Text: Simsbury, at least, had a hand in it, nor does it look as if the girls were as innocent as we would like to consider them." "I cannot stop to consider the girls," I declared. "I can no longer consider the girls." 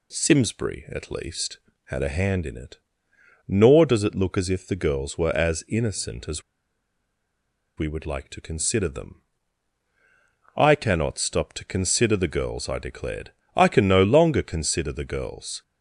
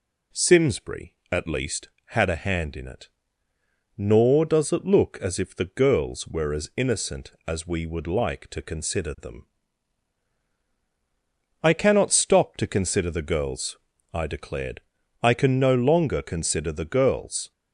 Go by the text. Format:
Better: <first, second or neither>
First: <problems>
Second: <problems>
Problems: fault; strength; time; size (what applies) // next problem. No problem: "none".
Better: second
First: pauses between "as" and "we"; strong; at 6.4 s; 1.3 s long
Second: none